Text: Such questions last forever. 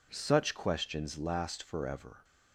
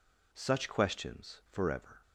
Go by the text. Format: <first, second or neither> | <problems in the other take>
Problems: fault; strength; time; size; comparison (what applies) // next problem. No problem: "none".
first | skips "last"; at 1.4 s